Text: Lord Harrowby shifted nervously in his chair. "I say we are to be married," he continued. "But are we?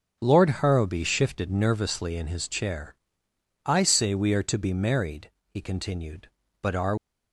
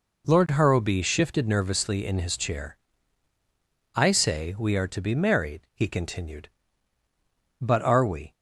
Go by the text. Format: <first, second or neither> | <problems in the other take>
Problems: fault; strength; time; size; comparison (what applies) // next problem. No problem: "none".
second | starts louder than the rest; until 1.2 s; 7 dB // stops before "we"; at 6.9 s